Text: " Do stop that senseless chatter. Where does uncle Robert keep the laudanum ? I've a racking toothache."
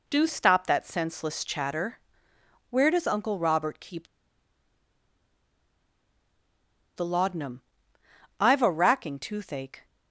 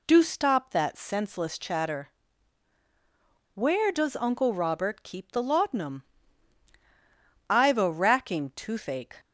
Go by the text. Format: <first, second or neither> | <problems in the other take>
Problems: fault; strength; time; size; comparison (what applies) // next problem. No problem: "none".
second | pauses between "keep" and "the"; strong; at 4.0 s; 2.8 s long